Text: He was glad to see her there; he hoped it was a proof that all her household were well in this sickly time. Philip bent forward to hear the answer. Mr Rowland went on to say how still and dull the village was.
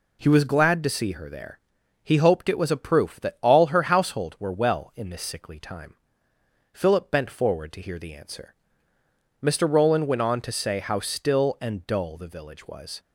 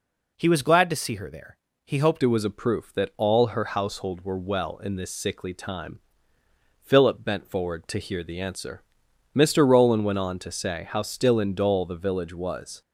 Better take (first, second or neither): first